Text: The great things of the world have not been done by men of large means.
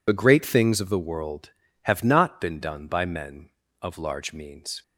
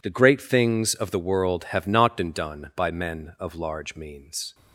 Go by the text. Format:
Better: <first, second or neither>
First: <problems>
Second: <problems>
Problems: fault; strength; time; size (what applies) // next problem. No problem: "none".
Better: second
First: loses the start of "The"; at 0.0 s; 35 ms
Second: none